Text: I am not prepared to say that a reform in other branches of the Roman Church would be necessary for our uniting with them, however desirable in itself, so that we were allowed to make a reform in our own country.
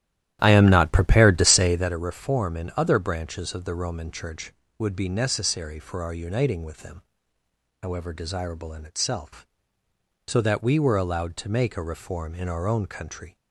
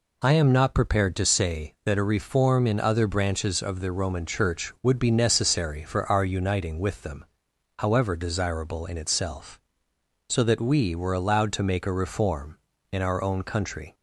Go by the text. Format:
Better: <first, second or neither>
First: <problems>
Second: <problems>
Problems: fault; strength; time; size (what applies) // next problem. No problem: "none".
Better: second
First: starts louder than the rest; strong; until 2.0 s; 12.5 dB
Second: none